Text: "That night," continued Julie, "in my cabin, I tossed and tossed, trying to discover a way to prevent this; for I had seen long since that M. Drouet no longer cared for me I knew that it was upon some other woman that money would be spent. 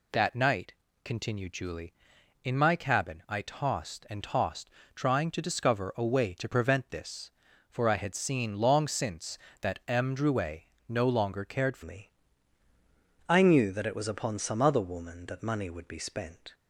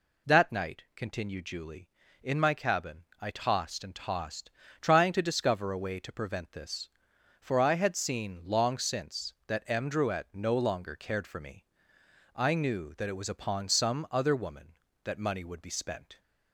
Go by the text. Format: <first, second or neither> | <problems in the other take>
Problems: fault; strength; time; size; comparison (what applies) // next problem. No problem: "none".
second | pauses between "Drouet" and "no"; slight; at 10.6 s; 0.26 s long // changes voice at "me"; from 11.8 s on; 4.7 s long // pauses between "me" and "I"; at 12.1 s; 1.1 s long; noticeable in the second